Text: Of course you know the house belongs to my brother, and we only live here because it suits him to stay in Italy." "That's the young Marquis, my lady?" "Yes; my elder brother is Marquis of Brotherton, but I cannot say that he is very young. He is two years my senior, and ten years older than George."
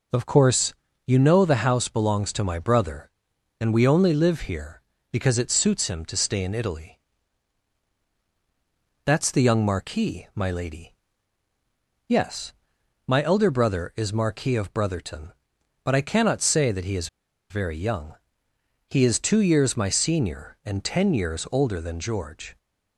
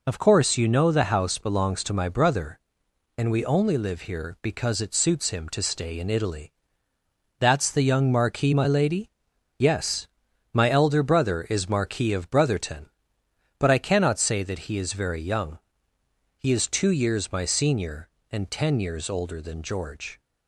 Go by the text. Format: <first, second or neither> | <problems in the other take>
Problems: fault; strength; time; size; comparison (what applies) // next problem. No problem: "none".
second | pauses between "course" and "you"; slight; at 0.7 s; 0.32 s long // pauses between "is" and "very"; at 17.0 s; 0.43 s long